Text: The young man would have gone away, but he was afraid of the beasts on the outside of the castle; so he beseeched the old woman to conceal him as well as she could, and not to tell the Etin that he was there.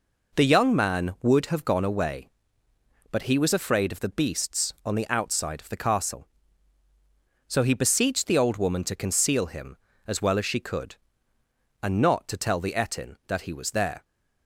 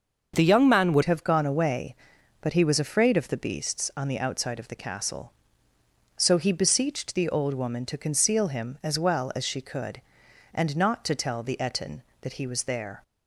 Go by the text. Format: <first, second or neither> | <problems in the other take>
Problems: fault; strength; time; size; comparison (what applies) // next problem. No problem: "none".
first | starts louder than the rest; until 1.3 s; 6.5 dB // changes voice at "have"; from 1.0 s on; 12.0 s long